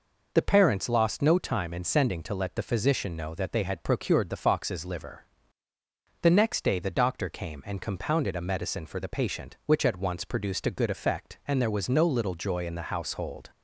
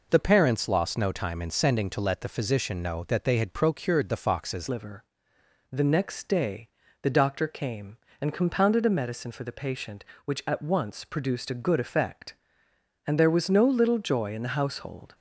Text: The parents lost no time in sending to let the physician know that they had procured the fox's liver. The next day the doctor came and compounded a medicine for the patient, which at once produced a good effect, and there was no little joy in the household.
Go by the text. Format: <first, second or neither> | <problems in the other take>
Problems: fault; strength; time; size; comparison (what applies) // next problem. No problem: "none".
first | changes voice at "liver"; from 4.6 s on; 10.5 s long // pauses between "day" and "the"; slight; at 6.6 s; 0.34 s long